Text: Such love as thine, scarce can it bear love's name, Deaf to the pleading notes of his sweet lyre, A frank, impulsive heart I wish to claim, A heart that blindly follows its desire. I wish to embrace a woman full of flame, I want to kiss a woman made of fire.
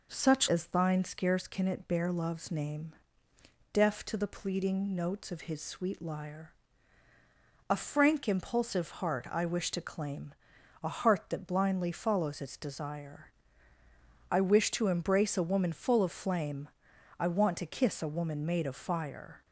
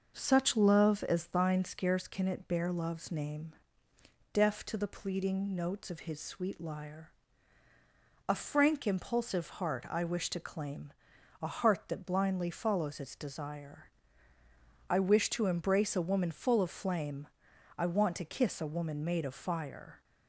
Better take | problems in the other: second | skips "love"; at 0.4 s

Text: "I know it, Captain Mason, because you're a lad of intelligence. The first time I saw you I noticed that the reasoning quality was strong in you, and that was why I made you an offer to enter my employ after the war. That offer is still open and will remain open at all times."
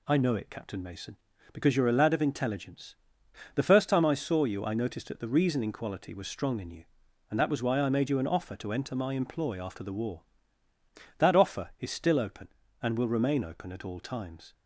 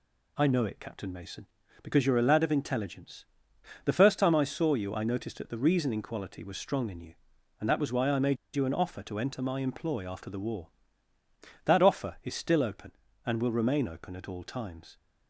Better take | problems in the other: first | pauses between "made" and "you"; slight; at 8.3 s; 0.19 s long

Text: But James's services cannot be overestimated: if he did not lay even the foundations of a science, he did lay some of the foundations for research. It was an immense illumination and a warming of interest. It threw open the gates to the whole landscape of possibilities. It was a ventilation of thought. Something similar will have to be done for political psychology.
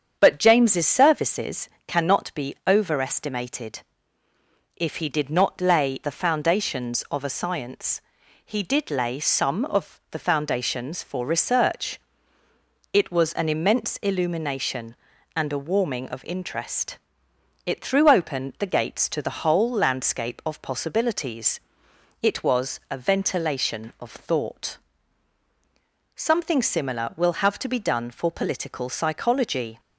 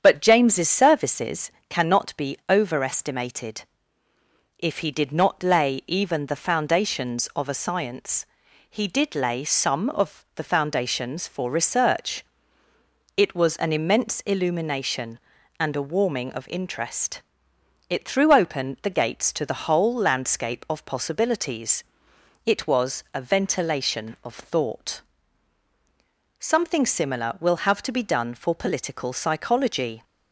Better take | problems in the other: second | starts louder than the rest; strong; until 1.2 s; 8 dB; strong in the second // pauses between "services" and "cannot"; slight; at 1.6 s; 0.18 s long; slight in the second // skips "even"; at 6.0 s

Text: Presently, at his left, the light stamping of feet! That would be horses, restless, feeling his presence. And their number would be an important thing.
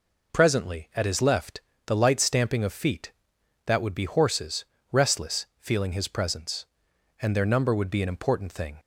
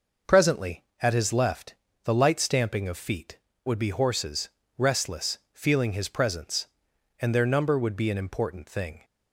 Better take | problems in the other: first | skips "That"; at 3.5 s

